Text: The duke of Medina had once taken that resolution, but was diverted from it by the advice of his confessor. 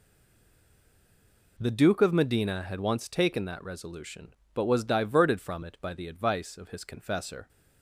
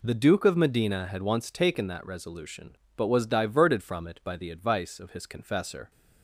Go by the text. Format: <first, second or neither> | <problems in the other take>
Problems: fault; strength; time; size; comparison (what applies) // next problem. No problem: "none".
second | stays silent before the first word; noticeable; until 1.5 s; 1.5 s long